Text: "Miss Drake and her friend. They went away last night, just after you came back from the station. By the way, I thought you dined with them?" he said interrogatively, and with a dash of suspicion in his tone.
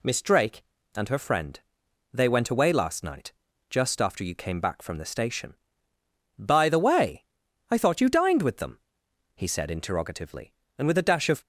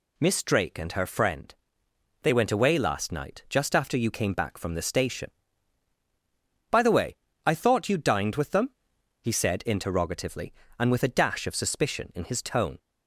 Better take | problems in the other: second | stops before "suspicion in his tone"; at 11.4 s

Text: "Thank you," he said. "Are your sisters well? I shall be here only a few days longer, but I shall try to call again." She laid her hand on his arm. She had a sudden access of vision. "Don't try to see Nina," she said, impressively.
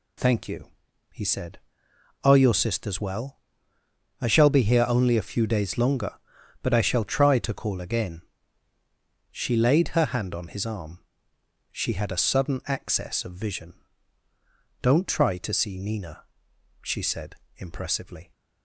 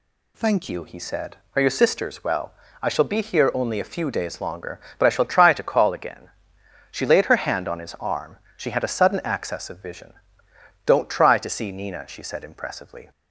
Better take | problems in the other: first | changes voice at "you"; from 0.6 s on; 12.5 s long

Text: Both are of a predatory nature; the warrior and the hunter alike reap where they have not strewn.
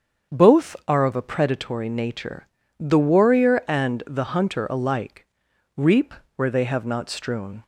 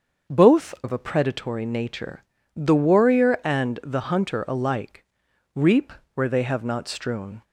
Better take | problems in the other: first | starts louder than the rest; until 1.4 s; 6.5 dB; strong in the first // skips "are"; at 0.7 s // pauses between "alike" and "reap"; noticeable; at 5.0 s; 0.48 s long; noticeable in the first // pauses between "reap" and "where"; slight; at 5.9 s; 0.22 s long; slight in the first

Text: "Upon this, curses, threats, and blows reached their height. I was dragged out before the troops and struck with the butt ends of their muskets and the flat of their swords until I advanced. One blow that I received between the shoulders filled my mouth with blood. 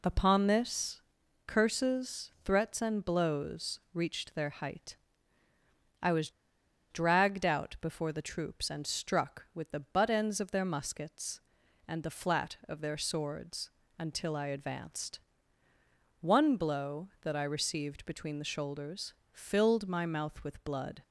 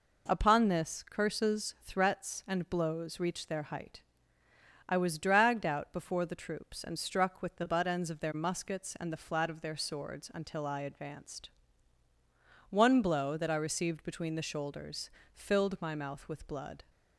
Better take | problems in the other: second | pauses between "was" and "dragged"; noticeable; at 6.3 s; 0.60 s long // pauses between "swords" and "until"; slight; at 13.7 s; 0.28 s long // pauses between "shoulders" and "filled"; slight; at 19.1 s; 0.20 s long; slight in the second

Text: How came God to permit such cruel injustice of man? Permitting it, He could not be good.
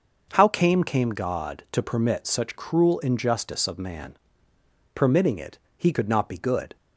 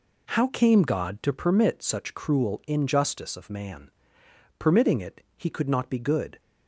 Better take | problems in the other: second | starts louder than the rest; noticeable; until 1.3 s; 6 dB // says "came" twice; at 0.8 s

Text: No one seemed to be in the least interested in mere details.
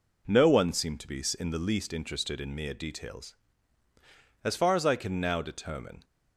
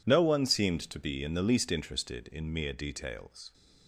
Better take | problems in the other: second | goes on to say "As far as I can now determine"; from 4.4 s on; 1.6 s long

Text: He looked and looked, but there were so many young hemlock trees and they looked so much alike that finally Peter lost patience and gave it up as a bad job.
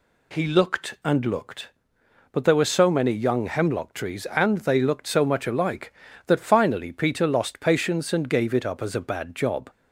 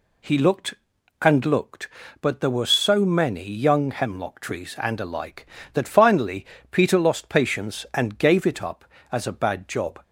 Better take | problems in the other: first | skips "they looked so much"; at 4.9 s // pauses between "finally" and "Peter"; slight; at 6.4 s; 0.24 s long

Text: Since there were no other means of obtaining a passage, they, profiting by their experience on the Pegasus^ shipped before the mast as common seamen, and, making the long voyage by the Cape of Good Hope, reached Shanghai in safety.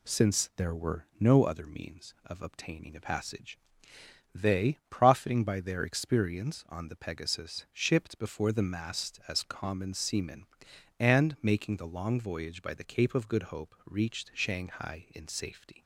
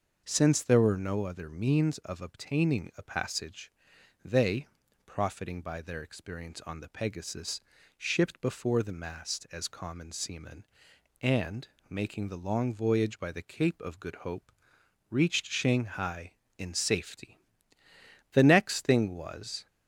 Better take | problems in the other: first | pauses between "Pegasus" and "shipped"; at 7.6 s; 0.38 s long // goes on to say "The next thing was"; from 18.3 s on; 1.3 s long

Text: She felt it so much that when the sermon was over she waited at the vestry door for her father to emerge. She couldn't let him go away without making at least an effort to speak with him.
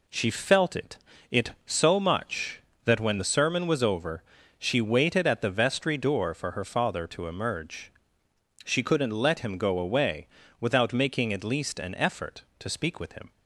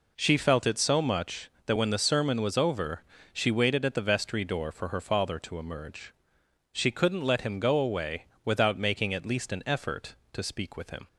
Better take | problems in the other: second | says "it" twice; at 1.2 s // pauses between "over" and "she"; at 4.2 s; 0.38 s long; slight in the second // pauses between "away" and "without"; slight; at 10.2 s; 0.32 s long; slight in the second

